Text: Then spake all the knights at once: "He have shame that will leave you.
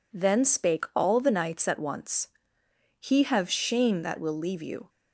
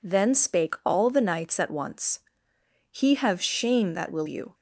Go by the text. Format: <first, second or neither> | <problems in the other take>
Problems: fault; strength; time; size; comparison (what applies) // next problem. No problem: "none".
first | skips "leave"; at 4.2 s